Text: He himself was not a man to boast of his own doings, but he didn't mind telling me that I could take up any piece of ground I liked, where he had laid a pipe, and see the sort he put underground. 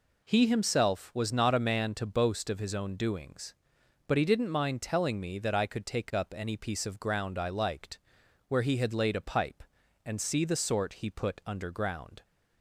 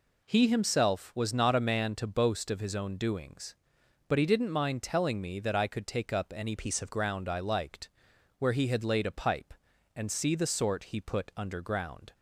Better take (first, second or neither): first